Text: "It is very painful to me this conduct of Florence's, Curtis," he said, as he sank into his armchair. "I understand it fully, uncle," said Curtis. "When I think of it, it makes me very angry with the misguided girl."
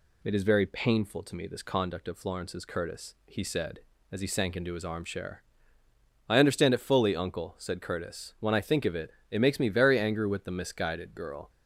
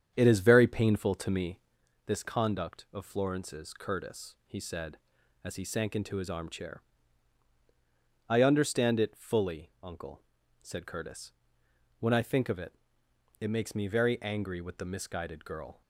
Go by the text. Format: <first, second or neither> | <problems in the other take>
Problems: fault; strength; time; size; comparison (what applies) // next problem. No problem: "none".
first | starts louder than the rest; strong; until 1.8 s; 8.5 dB // pauses between "me" and "this"; noticeable; at 1.5 s; 0.48 s long